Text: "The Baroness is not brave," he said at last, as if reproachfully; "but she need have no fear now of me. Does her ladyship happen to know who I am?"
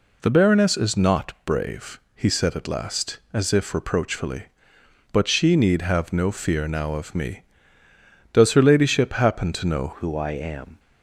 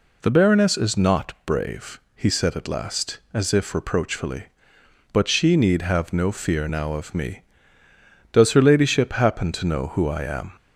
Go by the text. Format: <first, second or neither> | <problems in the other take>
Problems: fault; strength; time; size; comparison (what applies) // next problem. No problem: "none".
second | changes voice at "who"; from 9.9 s on; 0.8 s long